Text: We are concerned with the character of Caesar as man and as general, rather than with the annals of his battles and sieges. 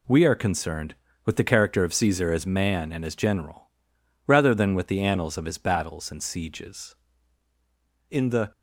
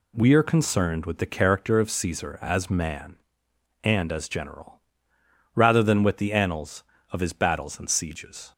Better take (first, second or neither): second